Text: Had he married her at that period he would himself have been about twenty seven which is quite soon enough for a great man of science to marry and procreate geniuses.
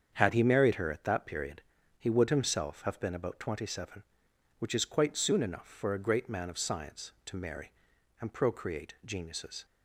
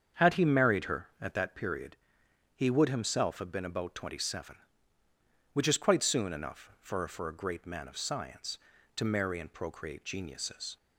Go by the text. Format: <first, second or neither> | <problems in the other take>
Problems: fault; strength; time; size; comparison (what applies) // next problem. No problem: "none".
first | starts louder than the rest; strong; until 1.3 s; 7.5 dB; strong in the first // pauses between "period" and "he"; noticeable; at 1.9 s; 0.58 s long; slight in the first // says "for" twice; at 7.0 s